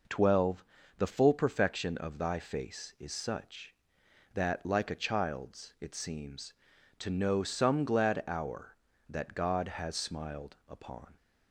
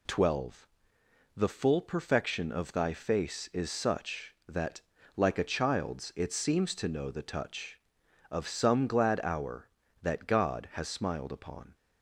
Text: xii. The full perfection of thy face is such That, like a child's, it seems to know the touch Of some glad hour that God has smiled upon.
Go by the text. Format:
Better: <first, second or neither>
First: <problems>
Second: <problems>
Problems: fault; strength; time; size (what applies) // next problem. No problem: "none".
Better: second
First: skips "the touch Of"; at 7.4 s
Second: none